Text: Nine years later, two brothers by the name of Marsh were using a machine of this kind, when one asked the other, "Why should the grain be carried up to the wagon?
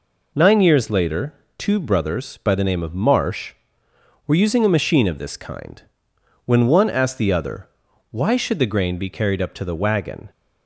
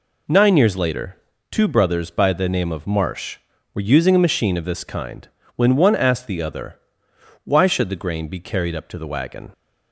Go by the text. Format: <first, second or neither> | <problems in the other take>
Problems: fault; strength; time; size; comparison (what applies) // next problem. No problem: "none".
neither | none